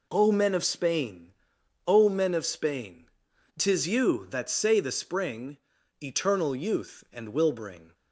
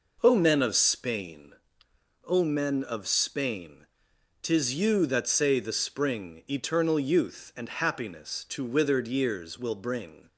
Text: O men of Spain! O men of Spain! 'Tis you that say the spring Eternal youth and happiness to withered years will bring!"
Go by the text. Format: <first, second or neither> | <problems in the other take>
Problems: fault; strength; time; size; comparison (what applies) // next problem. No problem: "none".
second | pauses between "spring" and "Eternal"; at 5.5 s; 0.42 s long // skips "happiness to withered years"; at 7.3 s